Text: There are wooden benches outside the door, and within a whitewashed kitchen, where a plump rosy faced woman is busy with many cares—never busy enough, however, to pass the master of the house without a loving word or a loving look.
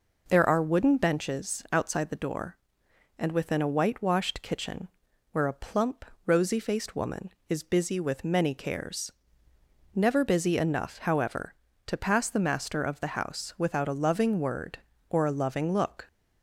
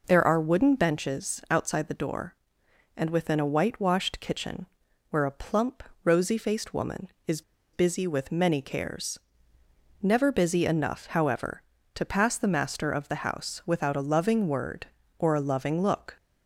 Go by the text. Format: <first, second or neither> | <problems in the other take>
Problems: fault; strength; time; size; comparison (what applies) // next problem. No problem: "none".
first | pauses between "plump" and "rosy"; slight; at 5.8 s; 0.20 s long; slight in the first // pauses between "is" and "busy"; slight; at 7.4 s; 0.32 s long